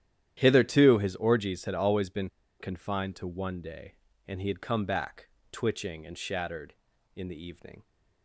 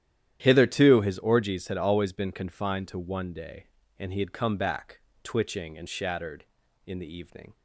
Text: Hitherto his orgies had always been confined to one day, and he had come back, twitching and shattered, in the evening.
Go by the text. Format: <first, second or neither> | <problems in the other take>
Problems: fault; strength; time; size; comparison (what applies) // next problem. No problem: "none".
second | starts louder than the rest; strong; until 1.3 s; 11 dB; strong in the second // pauses between "been" and "confined"; slight; at 2.2 s; 0.31 s long